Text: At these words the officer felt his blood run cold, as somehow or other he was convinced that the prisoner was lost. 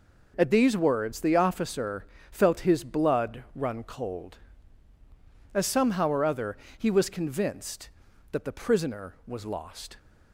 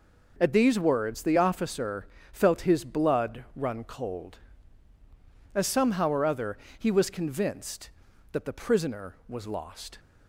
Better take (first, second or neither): neither